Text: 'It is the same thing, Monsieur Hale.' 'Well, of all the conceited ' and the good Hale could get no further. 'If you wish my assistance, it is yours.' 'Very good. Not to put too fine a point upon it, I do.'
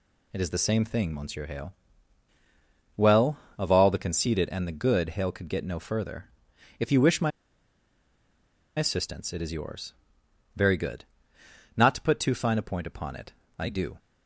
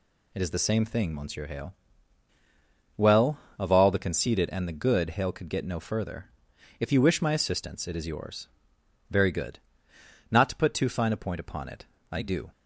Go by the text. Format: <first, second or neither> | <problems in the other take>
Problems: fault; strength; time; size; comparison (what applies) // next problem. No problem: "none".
second | pauses between "my" and "assistance"; strong; at 7.3 s; 1.4 s long